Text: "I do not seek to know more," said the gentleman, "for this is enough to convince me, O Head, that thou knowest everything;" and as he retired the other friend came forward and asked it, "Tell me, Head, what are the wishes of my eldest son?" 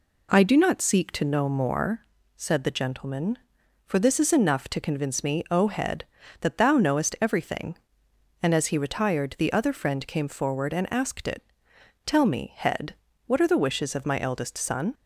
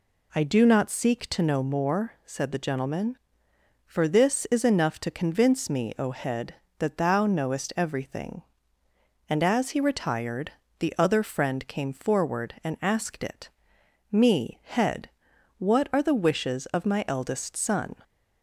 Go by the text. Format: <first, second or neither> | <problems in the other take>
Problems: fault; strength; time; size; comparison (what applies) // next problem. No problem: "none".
first | pauses between "retired" and "the"; slight; at 10.5 s; 0.26 s long // skips "Tell"; at 13.8 s